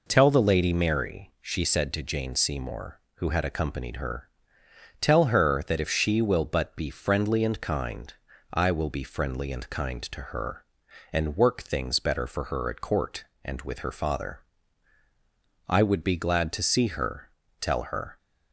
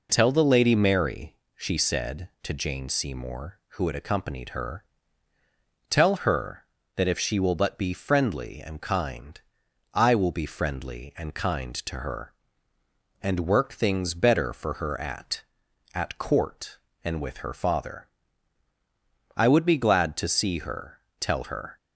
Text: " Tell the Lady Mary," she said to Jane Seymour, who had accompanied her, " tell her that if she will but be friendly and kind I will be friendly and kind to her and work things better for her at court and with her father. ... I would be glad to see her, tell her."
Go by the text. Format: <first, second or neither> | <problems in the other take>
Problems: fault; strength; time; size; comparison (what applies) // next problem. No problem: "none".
first | pauses between "kind" and "I"; noticeable; at 9.3 s; 0.54 s long; also in the first // says "at" twice; at 15.9 s